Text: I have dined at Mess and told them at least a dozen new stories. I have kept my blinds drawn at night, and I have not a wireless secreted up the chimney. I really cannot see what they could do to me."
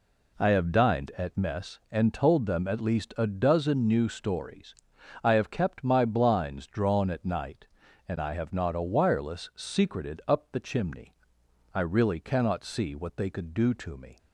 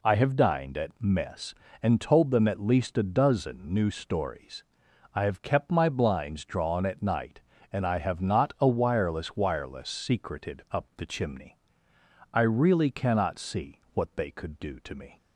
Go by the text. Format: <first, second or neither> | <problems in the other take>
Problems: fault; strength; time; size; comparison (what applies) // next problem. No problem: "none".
first | says "wireless" twice; at 9.3 s